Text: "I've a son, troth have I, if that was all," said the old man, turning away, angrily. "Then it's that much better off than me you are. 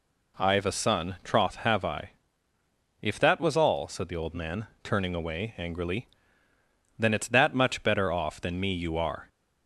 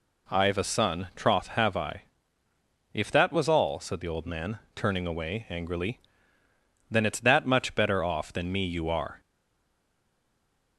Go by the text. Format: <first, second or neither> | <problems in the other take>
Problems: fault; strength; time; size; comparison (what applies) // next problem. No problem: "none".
first | stays silent after the last word; noticeable; from 9.1 s on; 1.6 s long